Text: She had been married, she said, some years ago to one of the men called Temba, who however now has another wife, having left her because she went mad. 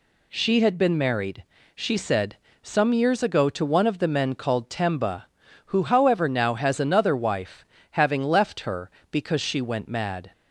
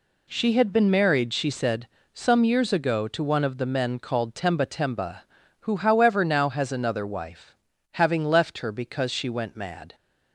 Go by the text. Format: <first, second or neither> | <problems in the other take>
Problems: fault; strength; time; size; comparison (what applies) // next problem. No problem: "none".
first | says "Temba" twice; at 4.6 s